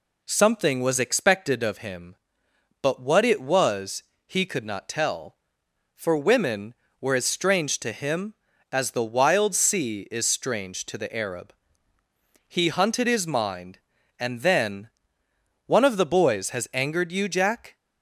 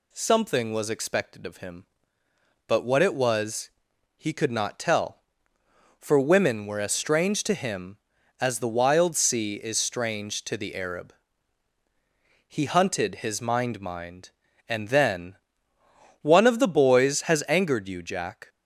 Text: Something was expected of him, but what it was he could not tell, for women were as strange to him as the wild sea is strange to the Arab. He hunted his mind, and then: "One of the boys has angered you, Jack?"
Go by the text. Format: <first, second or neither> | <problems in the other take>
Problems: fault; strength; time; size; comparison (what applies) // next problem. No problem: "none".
first | pauses between "was" and "he"; noticeable; at 3.7 s; 0.46 s long; slight in the first // says "mind" twice; at 13.8 s